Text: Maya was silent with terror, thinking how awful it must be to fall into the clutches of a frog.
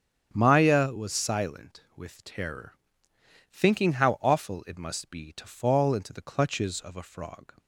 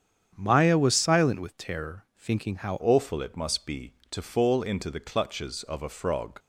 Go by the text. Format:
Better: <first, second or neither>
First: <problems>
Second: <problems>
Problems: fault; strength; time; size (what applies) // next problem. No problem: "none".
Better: first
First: starts louder than the rest; strong; until 1.3 s; 7.5 dB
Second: starts louder than the rest; strong; until 1.3 s; 8 dB // changes voice at "awful"; from 2.8 s on; 3.5 s long